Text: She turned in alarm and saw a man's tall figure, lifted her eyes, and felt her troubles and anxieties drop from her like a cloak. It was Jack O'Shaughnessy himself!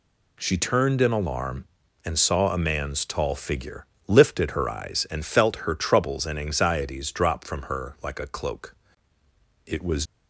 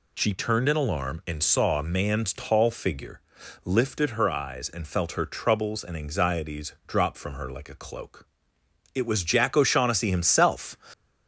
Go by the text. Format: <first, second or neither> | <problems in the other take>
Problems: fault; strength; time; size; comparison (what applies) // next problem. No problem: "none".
second | stops before "Jack O'Shaughnessy himself"; at 10.0 s